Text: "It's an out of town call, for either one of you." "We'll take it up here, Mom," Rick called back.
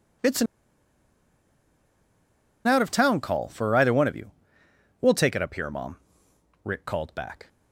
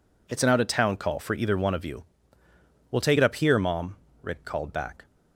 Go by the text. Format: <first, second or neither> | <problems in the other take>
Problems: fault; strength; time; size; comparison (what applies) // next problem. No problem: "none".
second | pauses between "an" and "out"; strong; at 0.4 s; 2.2 s long